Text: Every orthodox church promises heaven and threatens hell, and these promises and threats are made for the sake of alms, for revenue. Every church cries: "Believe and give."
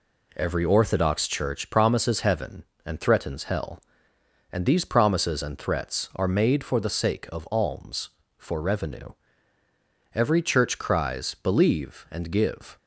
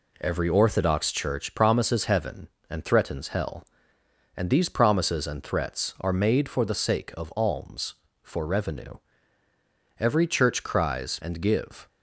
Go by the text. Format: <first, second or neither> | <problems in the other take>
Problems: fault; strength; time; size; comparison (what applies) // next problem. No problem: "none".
first | skips "Believe"; at 11.1 s